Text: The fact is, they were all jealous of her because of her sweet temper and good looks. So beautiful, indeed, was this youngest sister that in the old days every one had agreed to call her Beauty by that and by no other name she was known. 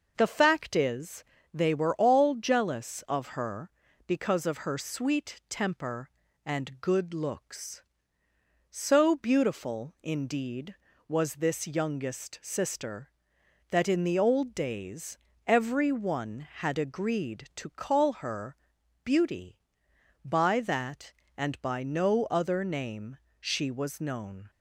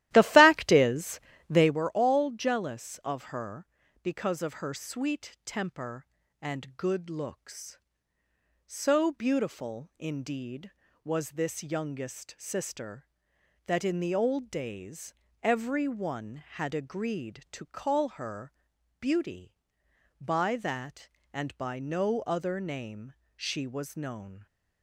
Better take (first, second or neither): first